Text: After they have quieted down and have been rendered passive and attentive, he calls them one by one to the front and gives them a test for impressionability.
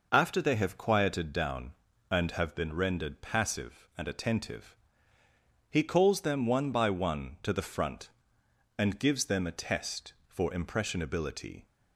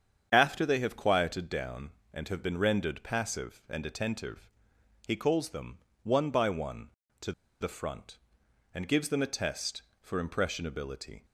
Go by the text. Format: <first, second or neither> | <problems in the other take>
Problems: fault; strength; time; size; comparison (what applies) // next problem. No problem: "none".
first | starts louder than the rest; strong; until 1.3 s; 8 dB // pauses between "them" and "one"; slight; at 5.7 s; 0.26 s long // pauses between "to" and "the"; slight; at 7.3 s; 0.29 s long